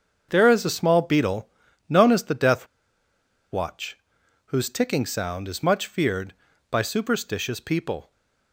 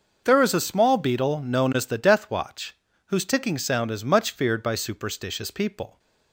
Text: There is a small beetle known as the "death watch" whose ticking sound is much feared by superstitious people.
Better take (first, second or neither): second